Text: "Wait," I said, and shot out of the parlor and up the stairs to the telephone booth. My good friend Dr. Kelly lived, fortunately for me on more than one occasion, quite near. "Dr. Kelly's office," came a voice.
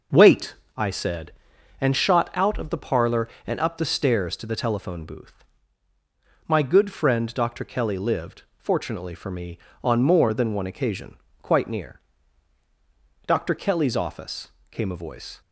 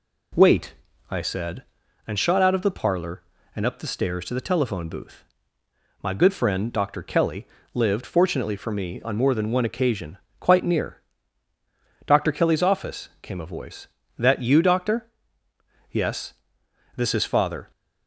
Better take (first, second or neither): first